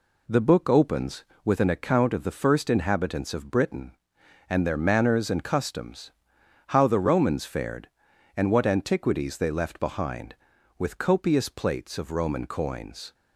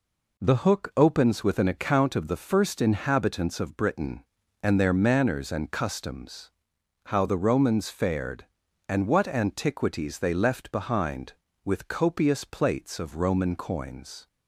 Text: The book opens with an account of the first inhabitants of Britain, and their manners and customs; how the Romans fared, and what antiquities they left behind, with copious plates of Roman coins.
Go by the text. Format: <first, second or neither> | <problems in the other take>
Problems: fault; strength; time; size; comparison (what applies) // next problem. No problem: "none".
first | says "hook" for "book"; at 0.5 s